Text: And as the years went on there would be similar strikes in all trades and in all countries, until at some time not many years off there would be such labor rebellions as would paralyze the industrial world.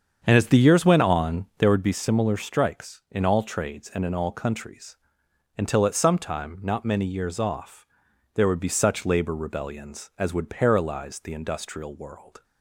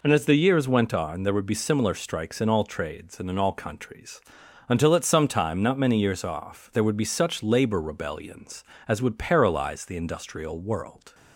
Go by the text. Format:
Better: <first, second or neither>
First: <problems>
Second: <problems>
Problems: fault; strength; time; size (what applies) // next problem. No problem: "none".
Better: second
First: starts louder than the rest; strong; until 1.8 s; 7.5 dB // pauses between "off" and "there"; noticeable; at 7.8 s; 0.50 s long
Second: none